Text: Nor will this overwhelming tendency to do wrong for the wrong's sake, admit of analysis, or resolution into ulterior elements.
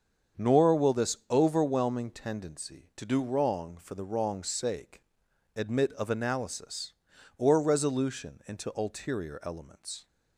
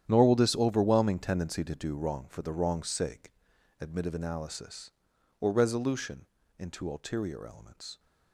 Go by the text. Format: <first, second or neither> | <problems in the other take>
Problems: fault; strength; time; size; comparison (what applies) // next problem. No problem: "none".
first | gets quieter; strong; throughout; 15 dB // starts louder than the rest; strong; until 1.0 s; 10 dB; strong in the first // pauses between "resolution" and "into"; slight; at 6.2 s; 0.34 s long